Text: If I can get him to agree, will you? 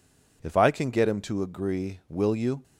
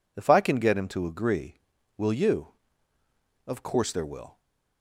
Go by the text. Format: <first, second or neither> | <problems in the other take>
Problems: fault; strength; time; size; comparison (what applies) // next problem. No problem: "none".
first | goes on to say "Of course there will"; noticeable; from 3.4 s on; 0.94 s long // stays silent after the last word; slight; from 4.3 s on; 0.5 s long